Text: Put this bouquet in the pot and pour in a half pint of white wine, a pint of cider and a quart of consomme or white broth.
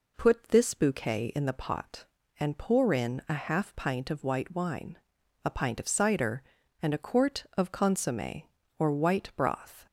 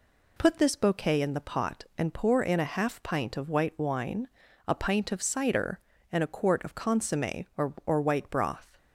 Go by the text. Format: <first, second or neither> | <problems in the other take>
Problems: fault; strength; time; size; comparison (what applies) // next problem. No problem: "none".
first | says "or" twice; at 7.8 s